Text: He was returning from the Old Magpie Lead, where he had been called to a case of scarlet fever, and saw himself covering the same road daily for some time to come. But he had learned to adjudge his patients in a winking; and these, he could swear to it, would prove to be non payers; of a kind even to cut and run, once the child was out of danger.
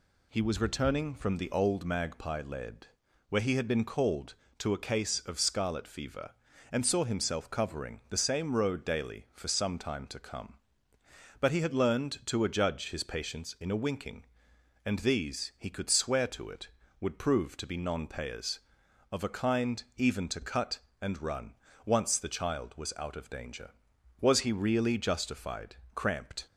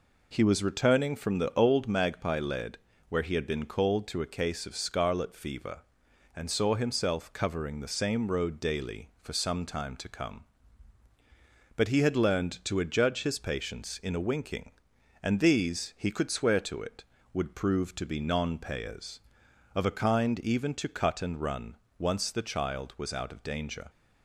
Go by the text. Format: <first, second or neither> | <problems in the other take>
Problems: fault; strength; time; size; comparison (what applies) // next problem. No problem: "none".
second | goes on to say "Was he really justified cramped"; strong; from 24.2 s on; 2.2 s long